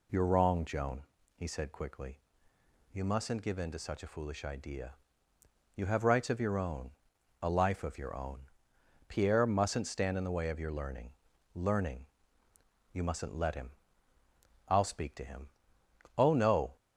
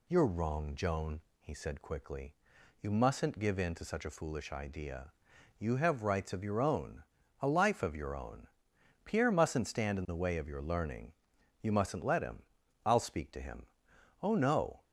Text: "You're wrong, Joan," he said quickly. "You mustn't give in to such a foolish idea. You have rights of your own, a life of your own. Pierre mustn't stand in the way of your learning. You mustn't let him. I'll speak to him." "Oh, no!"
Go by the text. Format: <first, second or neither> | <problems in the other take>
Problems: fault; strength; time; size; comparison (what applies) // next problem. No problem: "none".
second | says "learning" twice; at 11.5 s